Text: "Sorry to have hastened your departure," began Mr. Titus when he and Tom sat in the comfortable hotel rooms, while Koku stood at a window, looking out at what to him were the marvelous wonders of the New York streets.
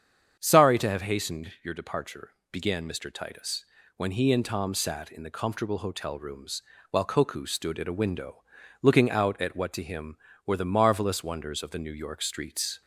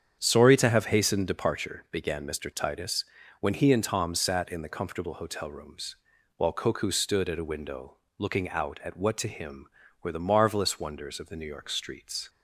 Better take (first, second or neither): first